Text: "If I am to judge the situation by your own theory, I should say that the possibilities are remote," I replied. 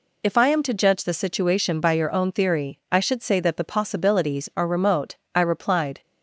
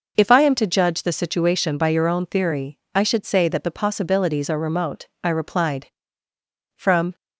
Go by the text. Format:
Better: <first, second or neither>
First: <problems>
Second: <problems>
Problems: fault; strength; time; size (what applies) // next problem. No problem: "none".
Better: first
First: none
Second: goes on to say "From"; slight; from 6.7 s on; 0.38 s long